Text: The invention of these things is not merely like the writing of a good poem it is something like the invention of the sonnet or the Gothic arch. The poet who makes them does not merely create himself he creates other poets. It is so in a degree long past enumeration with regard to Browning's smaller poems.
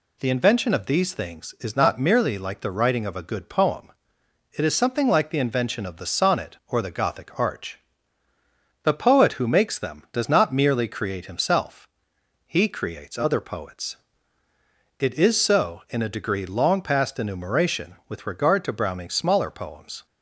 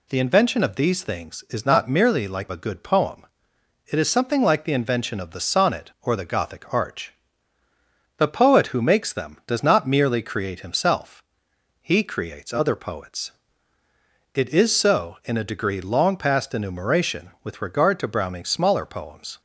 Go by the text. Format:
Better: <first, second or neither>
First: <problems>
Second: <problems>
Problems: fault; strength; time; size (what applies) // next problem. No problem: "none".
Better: first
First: pauses between "poem" and "it"; noticeable; at 3.9 s; 0.66 s long // pauses between "himself" and "he"; noticeable; at 11.8 s; 0.56 s long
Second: skips "the writing of"; at 2.5 s // pauses between "poem" and "it"; noticeable; at 3.2 s; 0.66 s long // pauses between "himself" and "he"; noticeable; at 11.2 s; 0.56 s long